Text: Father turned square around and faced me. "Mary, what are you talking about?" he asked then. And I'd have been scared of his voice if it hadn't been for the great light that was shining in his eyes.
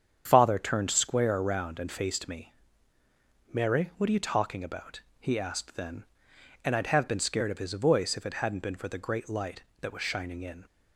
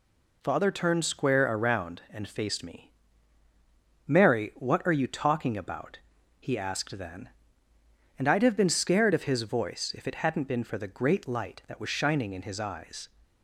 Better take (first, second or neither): second